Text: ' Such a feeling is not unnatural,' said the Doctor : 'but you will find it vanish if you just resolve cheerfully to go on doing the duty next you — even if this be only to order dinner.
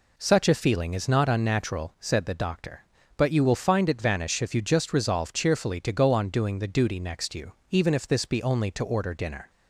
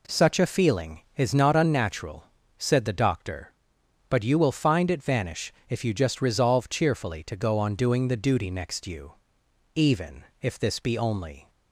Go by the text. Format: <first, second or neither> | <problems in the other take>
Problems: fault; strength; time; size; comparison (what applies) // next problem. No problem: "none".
first | pauses between "vanish" and "if"; slight; at 5.5 s; 0.16 s long // pauses between "even" and "if"; slight; at 10.2 s; 0.18 s long // stops before "to order dinner"; at 11.4 s